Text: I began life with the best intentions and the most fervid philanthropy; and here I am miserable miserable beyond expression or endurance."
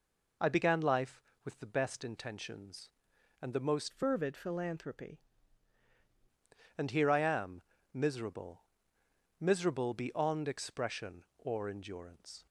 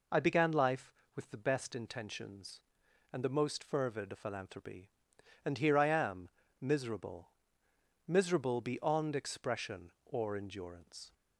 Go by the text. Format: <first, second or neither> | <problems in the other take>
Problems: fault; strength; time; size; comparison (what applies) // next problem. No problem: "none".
second | changes voice from "fervid" to "philanthropy"; from 3.9 to 5.2 s; 1.3 s long // pauses between "am" and "miserable"; slight; at 7.5 s; 0.32 s long; slight in the second // pauses between "miserable" and "miserable"; noticeable; at 8.6 s; 0.74 s long; noticeable in the second